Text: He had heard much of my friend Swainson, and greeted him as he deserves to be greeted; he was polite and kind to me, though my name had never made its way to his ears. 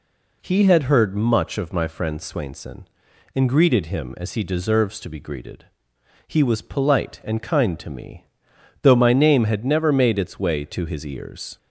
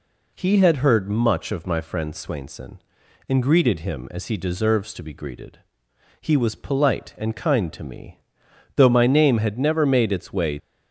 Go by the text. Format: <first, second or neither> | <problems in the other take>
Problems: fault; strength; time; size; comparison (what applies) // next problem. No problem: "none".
first | stops before "to his ears"; at 10.5 s